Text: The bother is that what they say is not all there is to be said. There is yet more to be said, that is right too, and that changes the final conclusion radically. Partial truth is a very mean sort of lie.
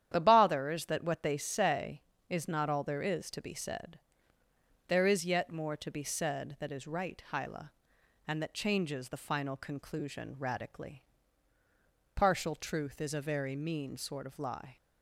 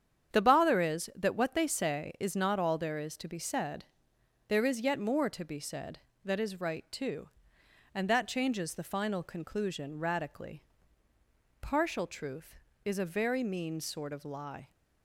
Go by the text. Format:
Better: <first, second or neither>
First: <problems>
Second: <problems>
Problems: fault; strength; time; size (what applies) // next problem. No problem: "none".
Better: second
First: starts louder than the rest; strong; until 1.1 s; 10 dB // says "hyla" for "too"; at 7.3 s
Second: starts louder than the rest; strong; until 1.3 s; 8.5 dB